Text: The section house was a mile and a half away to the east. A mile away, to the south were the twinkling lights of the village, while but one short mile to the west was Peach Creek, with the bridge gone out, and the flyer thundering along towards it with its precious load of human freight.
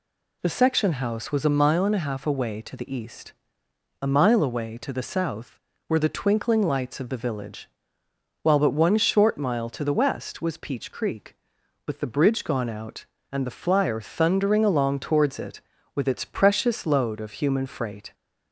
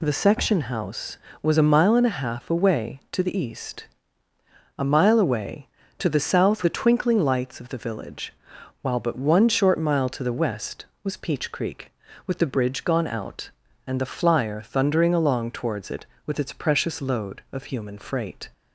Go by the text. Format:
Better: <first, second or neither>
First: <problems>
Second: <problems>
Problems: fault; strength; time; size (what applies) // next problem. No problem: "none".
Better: first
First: none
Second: skips "were"; at 6.6 s